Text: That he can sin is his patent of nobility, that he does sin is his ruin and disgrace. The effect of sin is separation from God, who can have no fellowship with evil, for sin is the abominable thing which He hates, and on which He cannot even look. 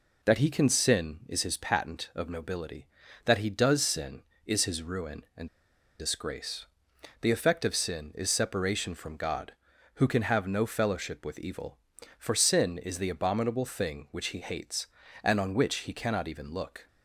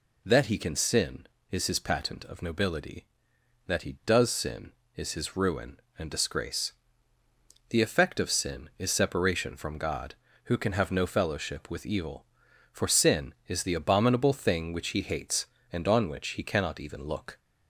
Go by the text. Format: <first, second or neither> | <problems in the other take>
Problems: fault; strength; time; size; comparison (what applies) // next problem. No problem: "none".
second | pauses between "and" and "disgrace"; noticeable; at 5.4 s; 0.51 s long